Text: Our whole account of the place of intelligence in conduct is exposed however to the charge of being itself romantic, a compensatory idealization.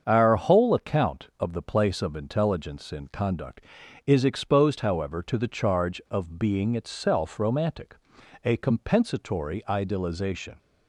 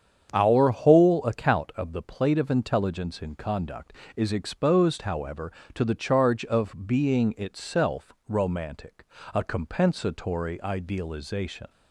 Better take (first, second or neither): first